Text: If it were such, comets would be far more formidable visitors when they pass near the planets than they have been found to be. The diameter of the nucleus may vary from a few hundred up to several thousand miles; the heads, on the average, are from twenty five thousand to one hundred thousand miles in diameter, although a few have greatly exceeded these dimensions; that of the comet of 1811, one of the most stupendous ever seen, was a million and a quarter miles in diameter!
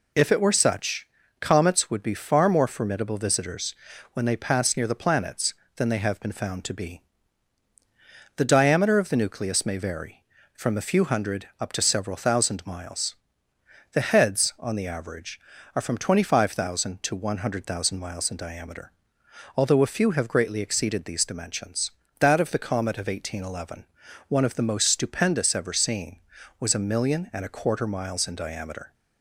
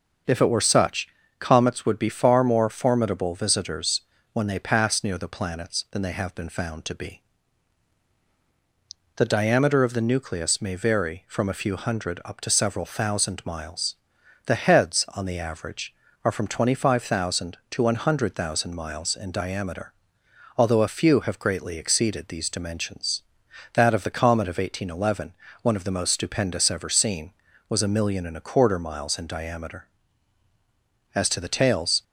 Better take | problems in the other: first | starts louder than the rest; until 1.5 s; 6.5 dB // pauses between "visitors" and "when"; slight; at 4.0 s; 0.32 s long; also in the first // goes on to say "As to the tails"; noticeable; from 31.1 s on; 0.90 s long

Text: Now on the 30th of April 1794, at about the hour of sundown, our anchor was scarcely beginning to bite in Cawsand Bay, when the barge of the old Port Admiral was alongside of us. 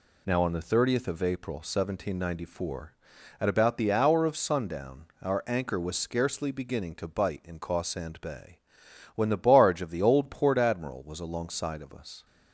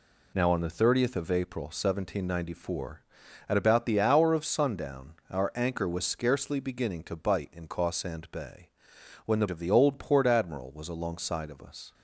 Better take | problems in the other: first | skips "barge"; at 9.4 s

